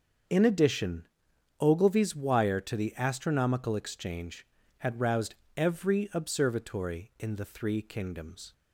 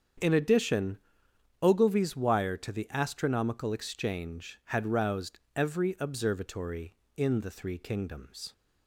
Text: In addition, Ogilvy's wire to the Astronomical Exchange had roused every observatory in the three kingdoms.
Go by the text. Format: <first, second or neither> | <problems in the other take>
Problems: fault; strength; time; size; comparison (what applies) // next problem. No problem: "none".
neither | starts louder than the rest; the same in both // pauses between "roused" and "every"; slight; the same in both